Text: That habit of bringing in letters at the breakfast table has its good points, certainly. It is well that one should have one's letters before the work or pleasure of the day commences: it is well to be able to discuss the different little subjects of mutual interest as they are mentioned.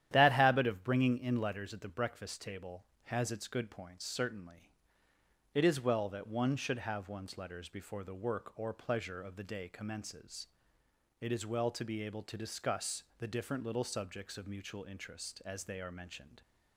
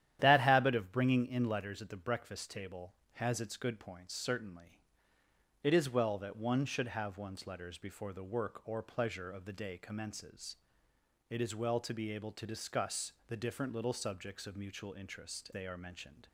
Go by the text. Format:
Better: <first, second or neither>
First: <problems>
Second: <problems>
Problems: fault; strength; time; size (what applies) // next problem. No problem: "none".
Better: first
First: starts louder than the rest; strong; until 1.1 s; 11 dB // pauses between "discuss" and "the"; slight; at 13.0 s; 0.16 s long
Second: starts louder than the rest; strong; until 1.2 s; 11 dB // pauses between "discuss" and "the"; slight; at 13.1 s; 0.16 s long // skips "as"; at 15.5 s